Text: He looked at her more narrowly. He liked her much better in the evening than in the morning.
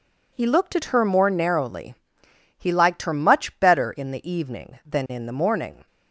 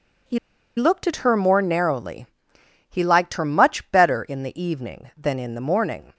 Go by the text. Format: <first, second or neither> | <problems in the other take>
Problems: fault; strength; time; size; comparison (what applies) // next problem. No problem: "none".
first | pauses between "He" and "looked"; at 0.3 s; 0.39 s long